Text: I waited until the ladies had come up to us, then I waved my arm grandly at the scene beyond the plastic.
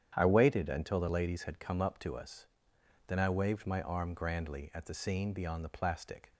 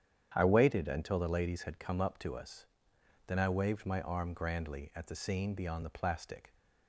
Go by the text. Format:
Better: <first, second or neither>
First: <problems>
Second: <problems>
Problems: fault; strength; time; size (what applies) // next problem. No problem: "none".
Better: neither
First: starts louder than the rest; strong; until 1.1 s; 9.5 dB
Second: starts louder than the rest; strong; until 1.3 s; 9.5 dB